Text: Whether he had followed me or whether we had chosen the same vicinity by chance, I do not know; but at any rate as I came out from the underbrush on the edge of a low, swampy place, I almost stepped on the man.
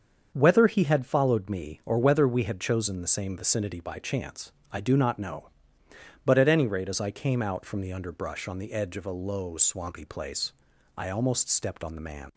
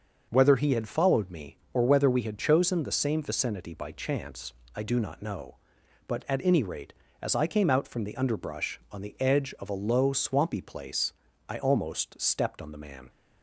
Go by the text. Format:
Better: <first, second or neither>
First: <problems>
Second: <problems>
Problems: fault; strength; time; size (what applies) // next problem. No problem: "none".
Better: neither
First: starts louder than the rest; until 1.3 s; 7 dB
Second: starts louder than the rest; until 1.3 s; 6.5 dB